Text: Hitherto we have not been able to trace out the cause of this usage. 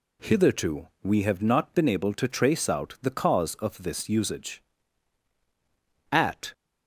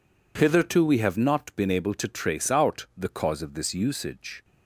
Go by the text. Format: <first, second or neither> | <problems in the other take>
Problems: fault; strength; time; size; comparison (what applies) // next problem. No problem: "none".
second | pauses between "Hitherto" and "we"; slight; at 0.8 s; 0.16 s long // goes on to say "At"; slight; from 6.1 s on; 0.40 s long